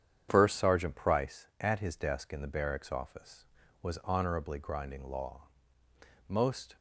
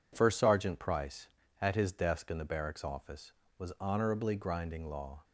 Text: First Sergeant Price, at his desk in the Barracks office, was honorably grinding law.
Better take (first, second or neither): second